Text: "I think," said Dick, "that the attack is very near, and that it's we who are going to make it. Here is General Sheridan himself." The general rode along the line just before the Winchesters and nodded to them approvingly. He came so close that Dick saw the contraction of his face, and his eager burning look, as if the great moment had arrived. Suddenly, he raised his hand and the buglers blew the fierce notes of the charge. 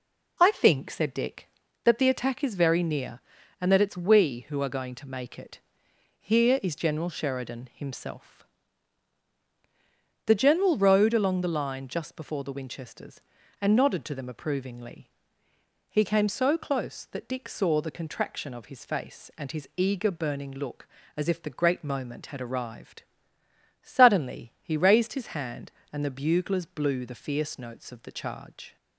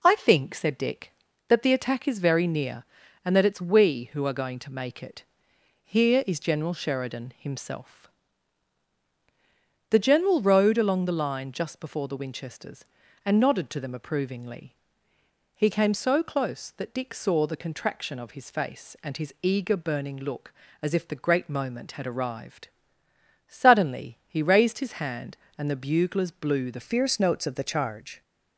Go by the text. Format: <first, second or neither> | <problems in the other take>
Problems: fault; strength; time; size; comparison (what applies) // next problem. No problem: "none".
first | changes voice at "fierce"; from 26.8 s on; 1.4 s long